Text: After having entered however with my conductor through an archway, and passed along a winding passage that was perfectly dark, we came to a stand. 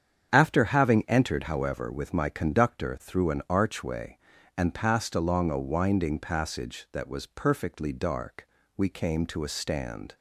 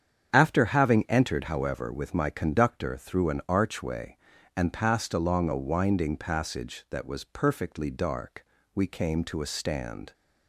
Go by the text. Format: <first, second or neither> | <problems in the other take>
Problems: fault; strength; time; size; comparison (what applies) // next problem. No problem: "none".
neither | starts louder than the rest; strong; the same in both